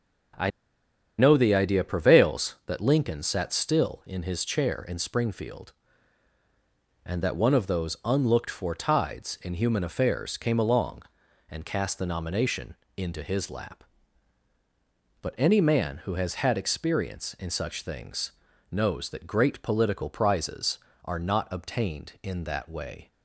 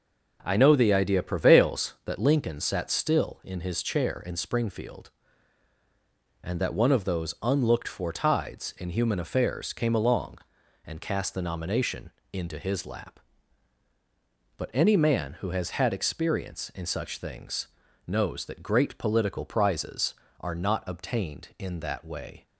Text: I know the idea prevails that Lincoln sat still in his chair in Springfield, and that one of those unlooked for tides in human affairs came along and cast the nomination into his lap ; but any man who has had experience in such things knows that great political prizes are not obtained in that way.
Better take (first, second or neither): second